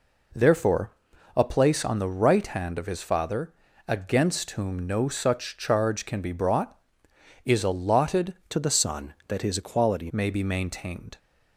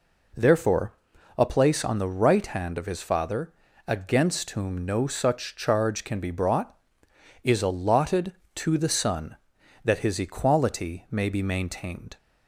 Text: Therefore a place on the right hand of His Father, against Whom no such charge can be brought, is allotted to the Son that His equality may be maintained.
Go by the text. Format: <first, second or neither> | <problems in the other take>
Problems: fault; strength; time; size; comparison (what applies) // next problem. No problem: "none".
second | pauses between "Therefore" and "a"; noticeable; at 0.9 s; 0.46 s long; noticeable in the second // changes voice from "to" to "equality"; from 8.5 to 10.0 s; 1.5 s long